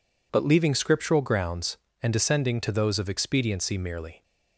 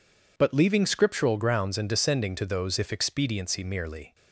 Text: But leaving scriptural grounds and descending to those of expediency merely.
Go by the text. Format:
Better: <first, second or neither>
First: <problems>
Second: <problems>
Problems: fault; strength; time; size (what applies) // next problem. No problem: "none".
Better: first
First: none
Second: says "if" for "of"; at 2.7 s